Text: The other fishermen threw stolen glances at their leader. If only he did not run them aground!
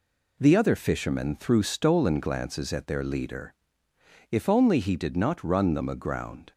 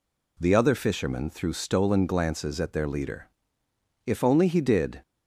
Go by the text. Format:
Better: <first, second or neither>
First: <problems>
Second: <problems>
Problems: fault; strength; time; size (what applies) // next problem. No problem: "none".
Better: first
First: none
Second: stops before "not run them aground"; at 5.0 s